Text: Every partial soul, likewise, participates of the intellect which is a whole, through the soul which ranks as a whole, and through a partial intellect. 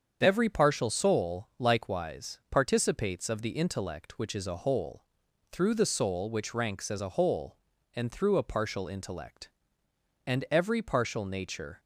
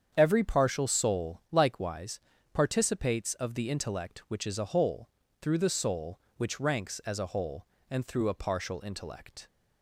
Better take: second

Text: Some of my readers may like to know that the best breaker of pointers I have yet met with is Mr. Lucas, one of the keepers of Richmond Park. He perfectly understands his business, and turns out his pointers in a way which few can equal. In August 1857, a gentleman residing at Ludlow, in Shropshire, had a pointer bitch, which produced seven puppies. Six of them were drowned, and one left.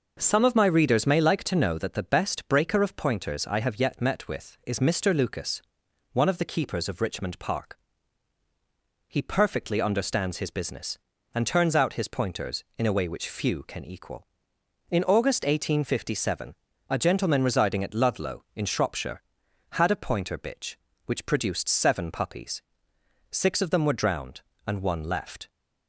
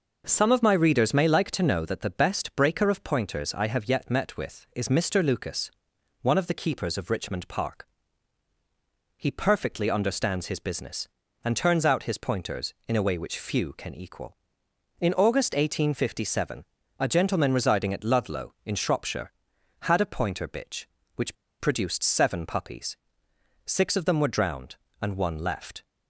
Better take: first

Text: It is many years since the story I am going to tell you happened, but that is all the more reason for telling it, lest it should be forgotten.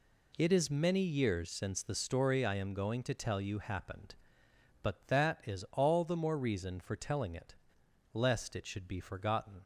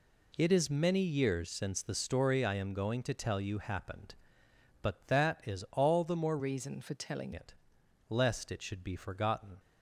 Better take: first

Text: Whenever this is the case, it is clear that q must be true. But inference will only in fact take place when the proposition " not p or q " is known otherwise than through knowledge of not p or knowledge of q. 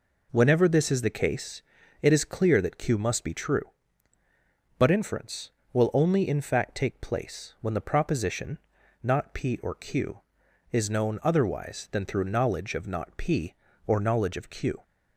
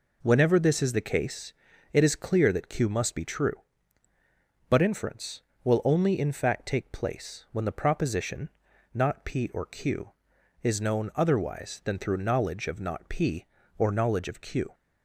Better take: neither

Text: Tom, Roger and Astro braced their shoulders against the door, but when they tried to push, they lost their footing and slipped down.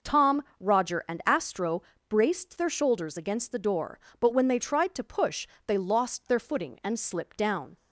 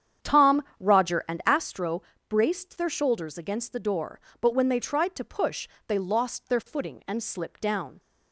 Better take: first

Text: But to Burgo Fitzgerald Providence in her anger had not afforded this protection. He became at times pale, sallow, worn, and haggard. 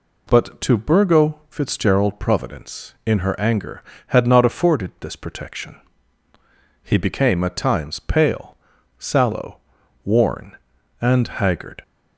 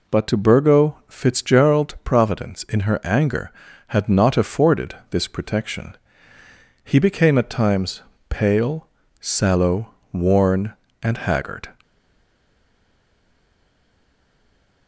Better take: first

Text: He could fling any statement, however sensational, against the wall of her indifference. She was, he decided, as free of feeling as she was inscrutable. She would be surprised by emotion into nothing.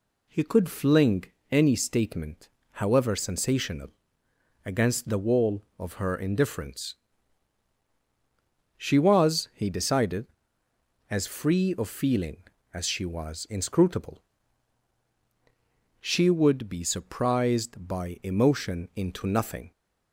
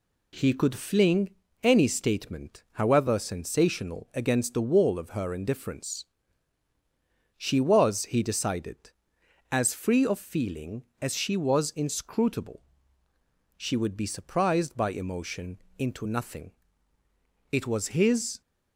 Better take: first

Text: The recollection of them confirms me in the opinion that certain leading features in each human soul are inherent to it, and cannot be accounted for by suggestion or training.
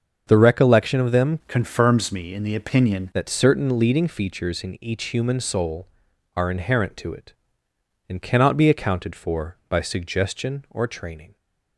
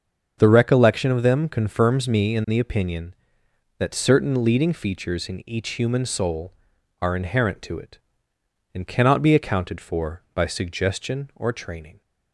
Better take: second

